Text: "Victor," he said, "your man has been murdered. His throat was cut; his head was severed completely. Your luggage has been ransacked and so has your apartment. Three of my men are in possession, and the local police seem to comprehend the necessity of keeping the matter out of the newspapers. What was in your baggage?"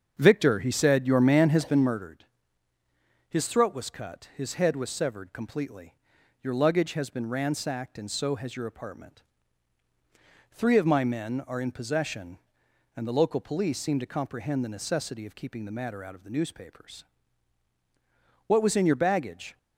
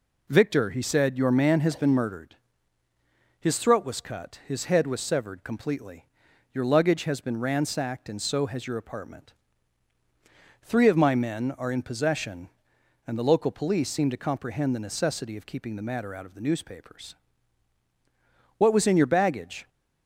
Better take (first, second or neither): second